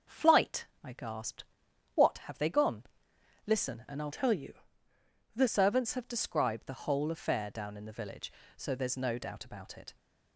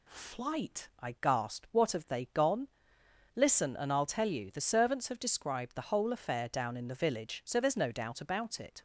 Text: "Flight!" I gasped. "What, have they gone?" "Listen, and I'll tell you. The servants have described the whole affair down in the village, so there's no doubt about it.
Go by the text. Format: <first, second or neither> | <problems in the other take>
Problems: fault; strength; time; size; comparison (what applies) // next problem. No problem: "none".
second | starts louder than the rest; until 1.2 s; 6.5 dB // changes voice from "tell" to "The"; from 4.1 to 5.4 s; 1.3 s long